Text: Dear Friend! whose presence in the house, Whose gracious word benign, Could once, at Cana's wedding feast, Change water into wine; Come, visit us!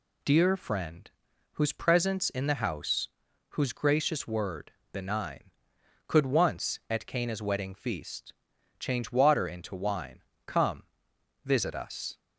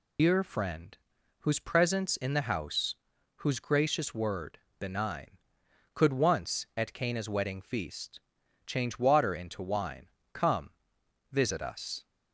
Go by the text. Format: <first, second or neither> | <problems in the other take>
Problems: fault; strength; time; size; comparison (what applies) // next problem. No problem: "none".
first | loses the start of "Dear"; at 0.1 s; 100 ms // pauses between "word" and "benign"; slight; at 4.5 s; 0.22 s long; slight in the first